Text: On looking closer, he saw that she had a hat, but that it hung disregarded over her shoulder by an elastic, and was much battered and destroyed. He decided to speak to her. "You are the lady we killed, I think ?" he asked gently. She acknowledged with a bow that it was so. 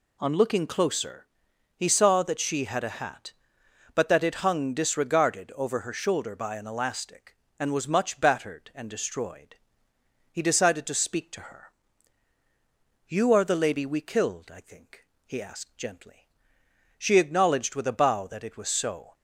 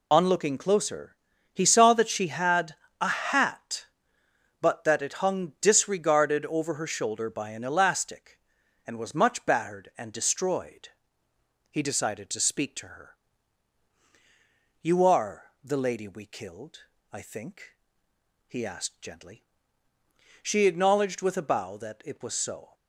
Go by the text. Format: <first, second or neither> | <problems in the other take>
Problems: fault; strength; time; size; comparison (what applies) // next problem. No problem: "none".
first | loses the start of "On"; at 0.1 s; 35 ms // pauses between "had" and "a"; slight; at 2.7 s; 0.24 s long